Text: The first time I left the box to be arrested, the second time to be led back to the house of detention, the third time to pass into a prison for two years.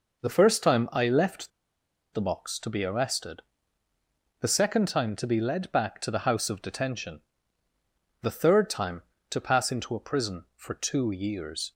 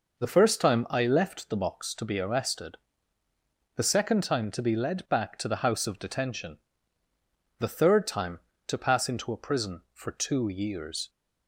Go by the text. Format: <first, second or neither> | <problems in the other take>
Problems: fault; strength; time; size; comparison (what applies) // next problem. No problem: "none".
second | pauses between "left" and "the"; noticeable; at 1.5 s; 0.63 s long